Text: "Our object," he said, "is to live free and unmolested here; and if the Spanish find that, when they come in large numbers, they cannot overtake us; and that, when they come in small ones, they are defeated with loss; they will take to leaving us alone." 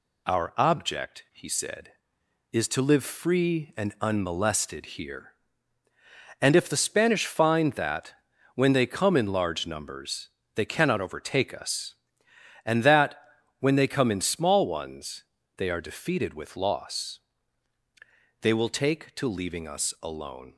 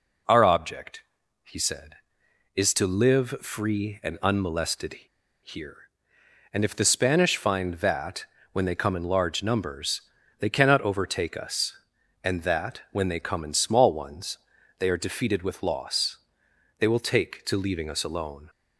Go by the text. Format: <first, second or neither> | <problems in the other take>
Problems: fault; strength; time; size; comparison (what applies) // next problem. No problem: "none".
first | pauses between "unmolested" and "here"; noticeable; at 4.9 s; 0.49 s long